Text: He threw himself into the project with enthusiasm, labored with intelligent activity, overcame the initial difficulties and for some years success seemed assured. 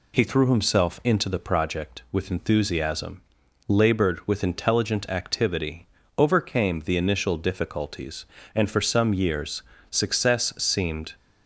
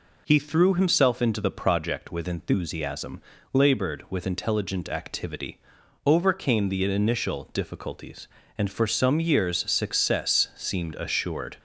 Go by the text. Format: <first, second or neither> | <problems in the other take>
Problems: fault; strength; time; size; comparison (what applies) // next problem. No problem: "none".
second | pauses between "years" and "success"; slight; at 9.6 s; 0.30 s long // stops before "assured"; at 11.1 s